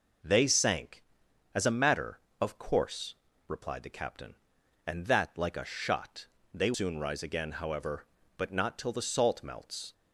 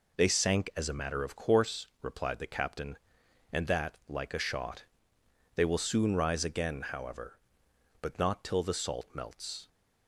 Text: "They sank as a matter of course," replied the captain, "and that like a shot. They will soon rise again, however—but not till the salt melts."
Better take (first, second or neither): second